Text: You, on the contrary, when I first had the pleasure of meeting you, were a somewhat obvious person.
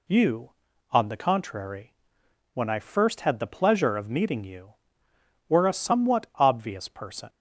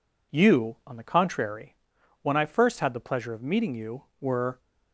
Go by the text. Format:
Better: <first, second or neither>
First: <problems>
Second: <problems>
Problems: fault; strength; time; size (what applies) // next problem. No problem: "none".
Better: first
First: none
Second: stops before "a somewhat obvious person"; at 4.5 s